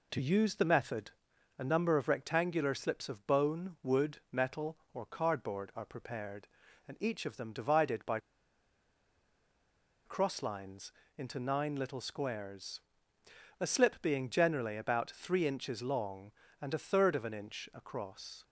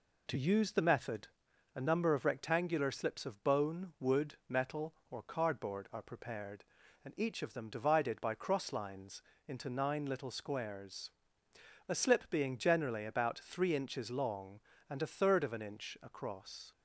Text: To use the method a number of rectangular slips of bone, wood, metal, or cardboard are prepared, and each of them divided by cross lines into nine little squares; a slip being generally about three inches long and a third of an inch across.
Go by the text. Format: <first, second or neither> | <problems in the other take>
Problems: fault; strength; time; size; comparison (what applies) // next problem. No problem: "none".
second | pauses between "method" and "a"; at 1.1 s; 0.44 s long; also in the second // pauses between "by" and "cross"; strong; at 8.1 s; 1.8 s long // pauses between "lines" and "into"; slight; at 10.9 s; 0.26 s long; slight in the second